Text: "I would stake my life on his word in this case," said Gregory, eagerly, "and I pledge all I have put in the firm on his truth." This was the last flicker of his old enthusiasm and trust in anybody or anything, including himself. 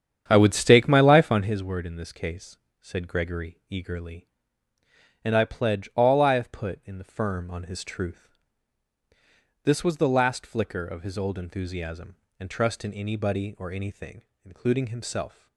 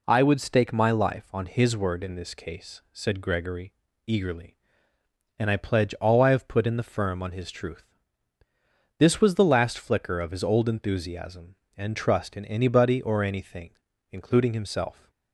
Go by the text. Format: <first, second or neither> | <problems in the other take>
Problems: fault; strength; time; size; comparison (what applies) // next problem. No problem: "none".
second | starts louder than the rest; strong; until 1.6 s; 8.5 dB